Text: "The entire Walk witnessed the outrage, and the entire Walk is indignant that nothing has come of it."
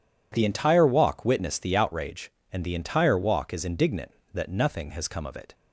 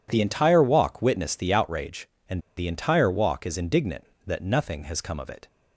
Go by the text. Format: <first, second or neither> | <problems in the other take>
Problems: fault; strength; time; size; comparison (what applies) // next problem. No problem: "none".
first | pauses between "and" and "the"; slight; at 2.4 s; 0.16 s long